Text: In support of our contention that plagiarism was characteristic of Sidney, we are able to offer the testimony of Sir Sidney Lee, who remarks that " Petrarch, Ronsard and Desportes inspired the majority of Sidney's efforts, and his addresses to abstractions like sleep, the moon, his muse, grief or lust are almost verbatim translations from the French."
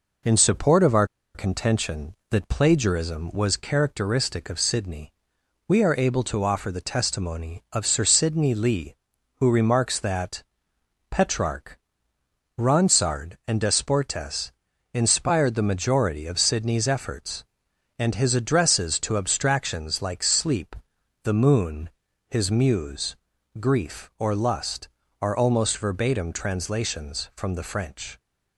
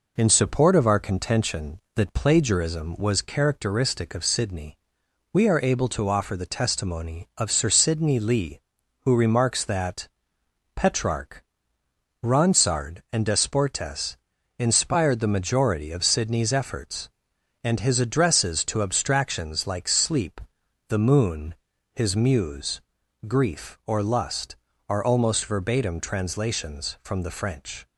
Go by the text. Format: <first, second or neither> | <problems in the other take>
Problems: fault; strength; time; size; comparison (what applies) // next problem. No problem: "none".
second | pauses between "our" and "contention"; slight; at 1.0 s; 0.28 s long // pauses between "Desportes" and "inspired"; at 14.5 s; 0.42 s long; also in the second